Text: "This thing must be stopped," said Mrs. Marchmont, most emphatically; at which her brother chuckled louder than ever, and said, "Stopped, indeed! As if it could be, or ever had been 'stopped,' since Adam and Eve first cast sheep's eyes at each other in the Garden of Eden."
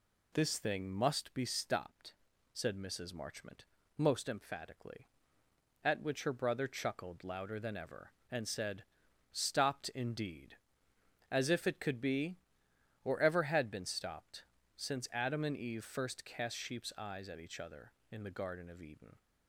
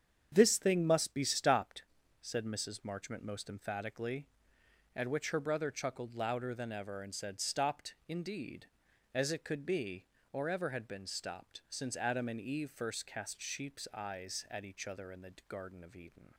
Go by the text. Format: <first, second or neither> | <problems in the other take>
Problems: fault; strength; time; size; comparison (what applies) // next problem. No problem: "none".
first | starts louder than the rest; strong; until 1.3 s; 8 dB // skips "if"; at 9.3 s